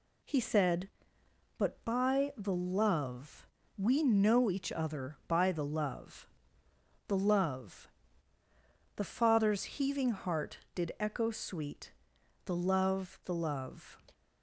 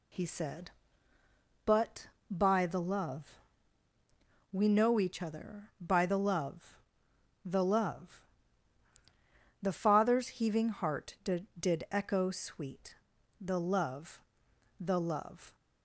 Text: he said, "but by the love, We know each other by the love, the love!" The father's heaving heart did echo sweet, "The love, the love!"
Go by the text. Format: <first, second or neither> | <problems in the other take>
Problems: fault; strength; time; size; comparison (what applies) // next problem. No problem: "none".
first | says "did" twice; at 11.5 s